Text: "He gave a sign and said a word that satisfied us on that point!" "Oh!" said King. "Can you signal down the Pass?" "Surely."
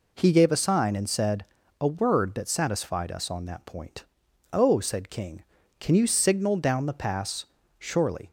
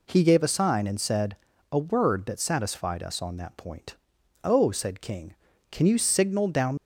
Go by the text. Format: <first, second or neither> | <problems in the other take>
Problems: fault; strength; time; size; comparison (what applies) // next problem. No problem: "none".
first | pauses between "said" and "a"; slight; at 1.3 s; 0.36 s long; slight in the first // stops before "the Pass Surely"; at 6.7 s